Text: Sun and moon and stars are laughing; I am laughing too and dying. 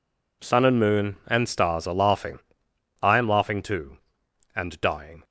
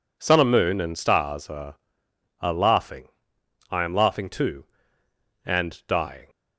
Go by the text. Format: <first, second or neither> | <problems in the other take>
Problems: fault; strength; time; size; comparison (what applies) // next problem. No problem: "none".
first | says "are" twice; at 2.4 s